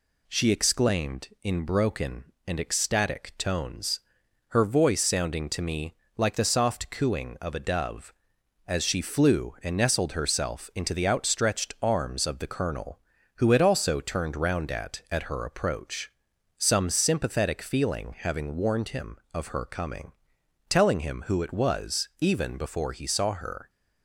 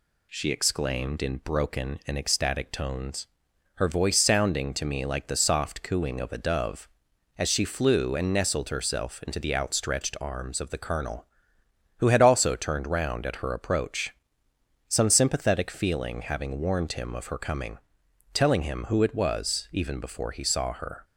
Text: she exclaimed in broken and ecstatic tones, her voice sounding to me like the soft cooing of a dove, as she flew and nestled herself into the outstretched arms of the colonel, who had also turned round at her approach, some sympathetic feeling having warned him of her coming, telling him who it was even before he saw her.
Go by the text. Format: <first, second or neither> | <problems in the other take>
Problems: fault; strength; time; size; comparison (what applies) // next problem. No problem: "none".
second | pauses between "me" and "like"; slight; at 5.9 s; 0.22 s long // says "at" twice; at 15.1 s